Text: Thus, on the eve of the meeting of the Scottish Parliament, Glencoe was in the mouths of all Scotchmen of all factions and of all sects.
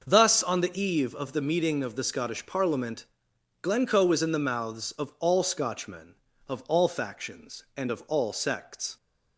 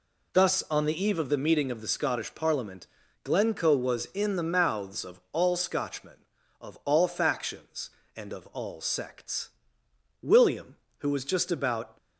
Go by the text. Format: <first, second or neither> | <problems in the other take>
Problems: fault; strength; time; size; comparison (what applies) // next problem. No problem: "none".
first | goes on to say "William who was just about"; strong; from 10.2 s on; 1.7 s long